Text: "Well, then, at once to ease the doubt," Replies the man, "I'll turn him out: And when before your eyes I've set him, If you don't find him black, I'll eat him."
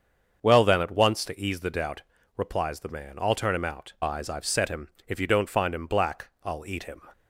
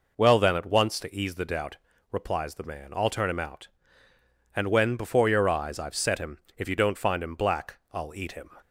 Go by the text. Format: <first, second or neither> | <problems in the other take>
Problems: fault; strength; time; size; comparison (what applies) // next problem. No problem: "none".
second | starts louder than the rest; until 1.4 s; 7 dB // skips "And when before your"; at 3.9 s